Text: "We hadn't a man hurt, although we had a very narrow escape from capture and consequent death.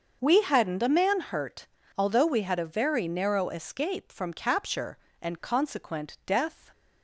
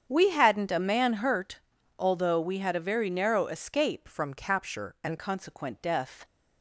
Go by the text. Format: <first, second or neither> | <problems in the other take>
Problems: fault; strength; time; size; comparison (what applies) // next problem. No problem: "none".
first | starts louder than the rest; strong; until 1.0 s; 8 dB; also in the first // changes voice from "from" to "and"; from 4.0 to 5.1 s; 1.1 s long